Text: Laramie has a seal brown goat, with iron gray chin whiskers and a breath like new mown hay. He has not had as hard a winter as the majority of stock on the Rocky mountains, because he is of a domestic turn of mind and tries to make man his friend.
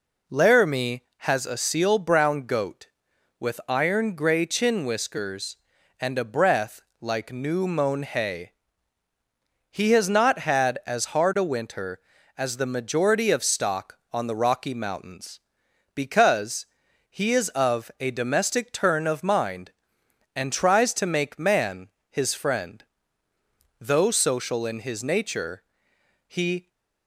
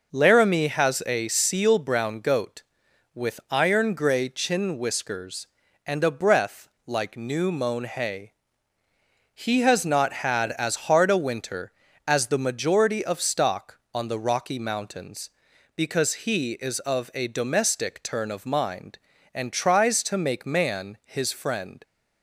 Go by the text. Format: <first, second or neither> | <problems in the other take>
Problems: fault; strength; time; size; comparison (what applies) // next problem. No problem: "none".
second | pauses between "breath" and "like"; slight; at 6.8 s; 0.20 s long; slight in the second // pauses between "because" and "he"; at 16.6 s; 0.42 s long // pauses between "man" and "his"; slight; at 21.8 s; 0.22 s long // goes on to say "Though social in his nature he"; strong; from 23.7 s on; 2.8 s long